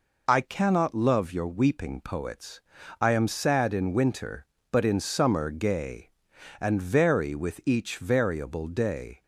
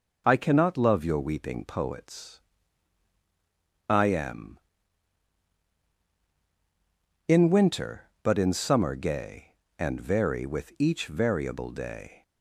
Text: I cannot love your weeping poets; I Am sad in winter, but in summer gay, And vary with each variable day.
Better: first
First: none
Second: skips "sad"; at 5.9 s

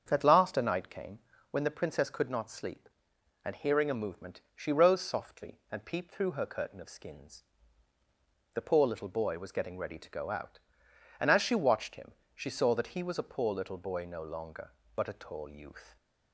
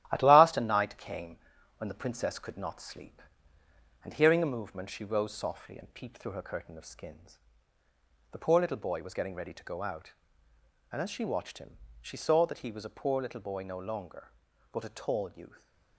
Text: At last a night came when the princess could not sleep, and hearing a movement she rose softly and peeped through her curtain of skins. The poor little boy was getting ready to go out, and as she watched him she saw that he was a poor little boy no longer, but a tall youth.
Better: first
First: starts louder than the rest; strong; until 1.1 s; 7.5 dB // pauses between "came" and "when"; slight; at 1.1 s; 0.32 s long // pauses between "him" and "she"; slight; at 12.1 s; 0.24 s long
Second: gets quieter; noticeable; throughout; 5 dB // starts louder than the rest; strong; until 1.1 s; 13.5 dB // pauses between "came" and "when"; at 1.3 s; 0.42 s long // pauses between "him" and "she"; slight; at 11.7 s; 0.26 s long

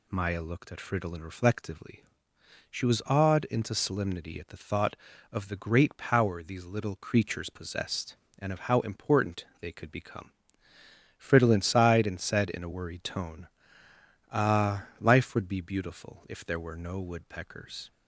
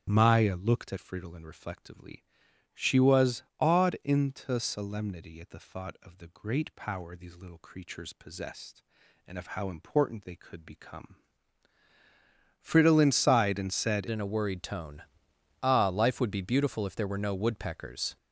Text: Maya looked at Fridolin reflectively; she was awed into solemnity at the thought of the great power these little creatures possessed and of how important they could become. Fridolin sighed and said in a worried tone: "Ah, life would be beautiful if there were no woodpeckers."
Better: first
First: none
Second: starts louder than the rest; strong; until 1.1 s; 8.5 dB // pauses between "was" and "awed"; slight; at 3.4 s; 0.16 s long // changes voice at "in"; from 14.1 s on; 4.0 s long

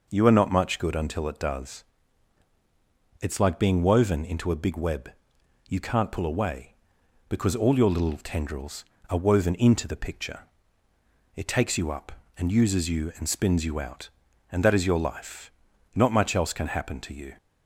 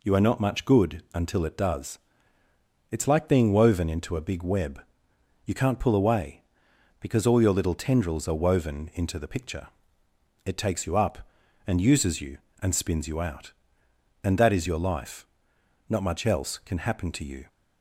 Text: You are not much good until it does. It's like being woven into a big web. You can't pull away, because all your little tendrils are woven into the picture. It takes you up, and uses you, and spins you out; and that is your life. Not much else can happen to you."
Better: neither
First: none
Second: none

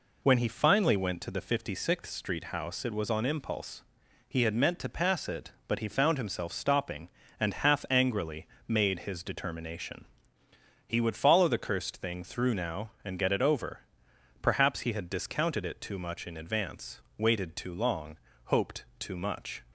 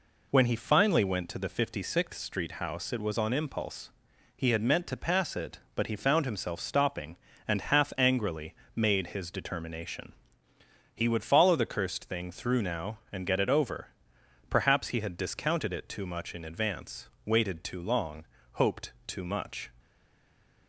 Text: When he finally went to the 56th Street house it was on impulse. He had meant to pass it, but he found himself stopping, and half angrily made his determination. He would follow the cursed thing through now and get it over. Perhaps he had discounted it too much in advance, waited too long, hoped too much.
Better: first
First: pauses between "angrily" and "made"; slight; at 8.4 s; 0.22 s long // pauses between "hoped" and "too"; slight; at 18.8 s; 0.16 s long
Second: pauses between "angrily" and "made"; slight; at 8.5 s; 0.22 s long // pauses between "hoped" and "too"; slight; at 18.9 s; 0.16 s long // stays silent after the last word; slight; from 19.7 s on; 0.9 s long

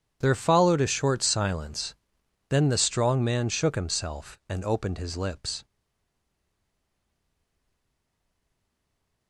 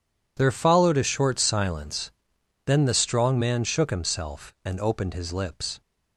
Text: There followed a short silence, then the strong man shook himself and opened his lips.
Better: second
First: stays silent after the last word; strong; from 5.6 s on; 3.6 s long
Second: none

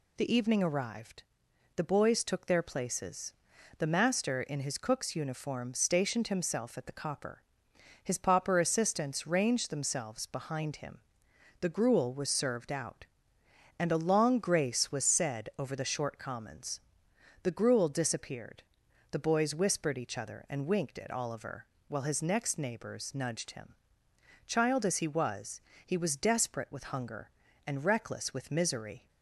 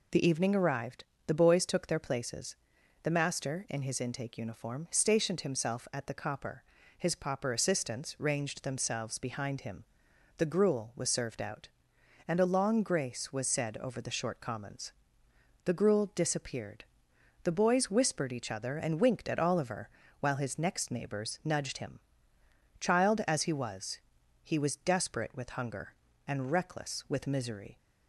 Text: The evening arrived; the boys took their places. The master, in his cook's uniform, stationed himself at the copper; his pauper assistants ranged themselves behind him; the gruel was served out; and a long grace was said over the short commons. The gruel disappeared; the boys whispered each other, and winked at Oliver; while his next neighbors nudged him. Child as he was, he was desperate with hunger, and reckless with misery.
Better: first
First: none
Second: says "intake" for "cook's"; at 3.9 s

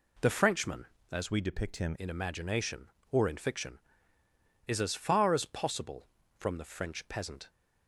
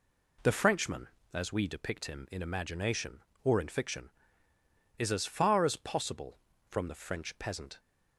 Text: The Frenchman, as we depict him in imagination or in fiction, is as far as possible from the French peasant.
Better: second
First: changes voice from "we" to "him"; from 1.3 to 1.9 s; 0.6 s long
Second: none

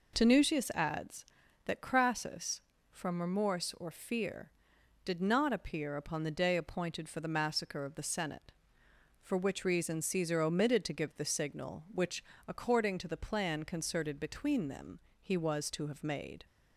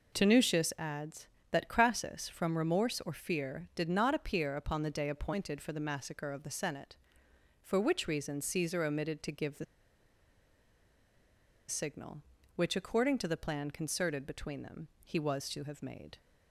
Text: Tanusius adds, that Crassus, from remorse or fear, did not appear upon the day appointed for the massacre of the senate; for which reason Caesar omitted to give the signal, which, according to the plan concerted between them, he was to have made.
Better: first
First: none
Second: pauses between "the" and "signal"; strong; at 9.6 s; 2.0 s long

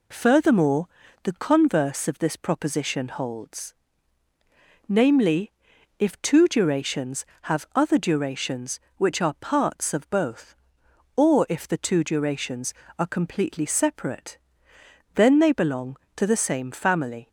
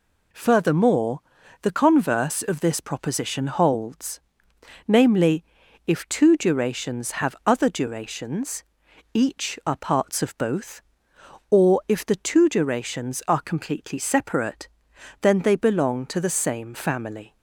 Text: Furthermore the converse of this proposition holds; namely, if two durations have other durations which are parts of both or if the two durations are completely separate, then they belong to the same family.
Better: first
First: pauses between "Furthermore" and "the"; slight; at 0.8 s; 0.36 s long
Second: pauses between "Furthermore" and "the"; at 1.2 s; 0.40 s long // says "each" for "which"; at 9.1 s

